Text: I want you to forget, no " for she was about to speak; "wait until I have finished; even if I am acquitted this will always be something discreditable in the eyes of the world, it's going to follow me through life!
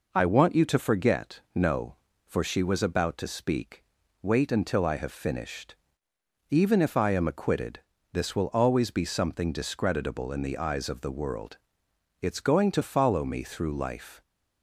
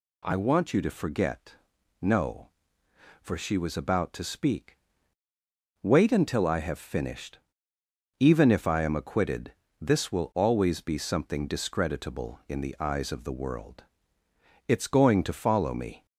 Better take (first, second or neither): first